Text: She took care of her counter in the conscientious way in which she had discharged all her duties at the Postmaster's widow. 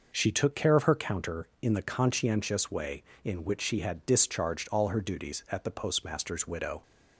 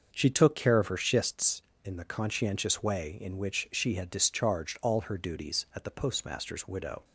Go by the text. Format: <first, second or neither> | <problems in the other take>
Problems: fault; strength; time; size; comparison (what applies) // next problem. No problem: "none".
first | starts louder than the rest; until 1.1 s; 6.5 dB // says "schists" for "counter"; at 0.9 s